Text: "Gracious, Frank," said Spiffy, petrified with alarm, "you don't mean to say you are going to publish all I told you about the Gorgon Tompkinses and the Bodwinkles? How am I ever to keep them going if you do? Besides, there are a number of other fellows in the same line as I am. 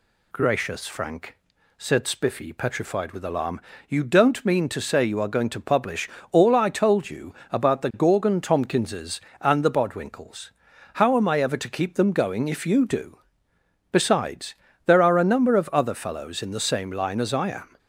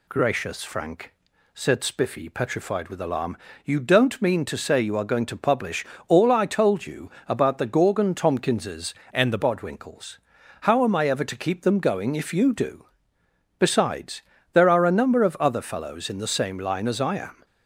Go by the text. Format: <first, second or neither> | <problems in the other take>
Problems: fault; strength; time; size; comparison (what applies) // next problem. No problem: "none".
first | pauses between "publish" and "all"; slight; at 5.8 s; 0.22 s long; slight in the first // pauses between "you" and "about"; slight; at 7.1 s; 0.16 s long; slight in the first // changes voice from "and" to "the"; from 9.1 to 9.3 s; 0.2 s long